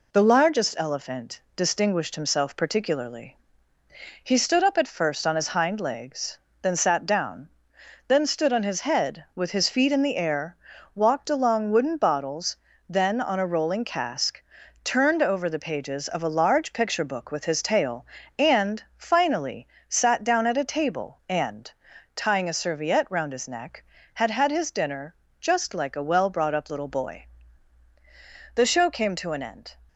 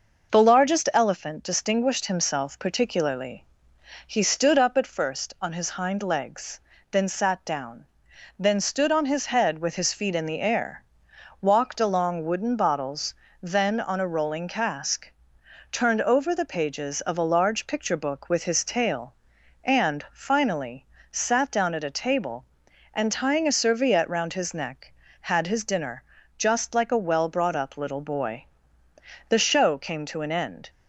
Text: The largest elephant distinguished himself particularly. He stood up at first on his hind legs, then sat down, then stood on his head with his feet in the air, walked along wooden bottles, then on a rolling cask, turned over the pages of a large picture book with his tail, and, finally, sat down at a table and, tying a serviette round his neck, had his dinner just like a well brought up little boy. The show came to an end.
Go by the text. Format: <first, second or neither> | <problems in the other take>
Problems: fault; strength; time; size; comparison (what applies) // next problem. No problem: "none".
second | says "had" twice; at 24.3 s // pauses between "dinner" and "just"; slight; at 25.1 s; 0.24 s long; slight in the second